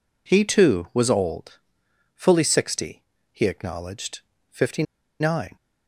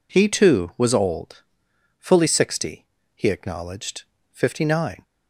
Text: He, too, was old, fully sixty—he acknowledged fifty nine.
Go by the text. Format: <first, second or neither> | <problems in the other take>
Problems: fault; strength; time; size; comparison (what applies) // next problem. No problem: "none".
second | pauses between "acknowledged" and "fifty"; slight; at 4.1 s; 0.32 s long; slight in the second // pauses between "fifty" and "nine"; at 4.8 s; 0.37 s long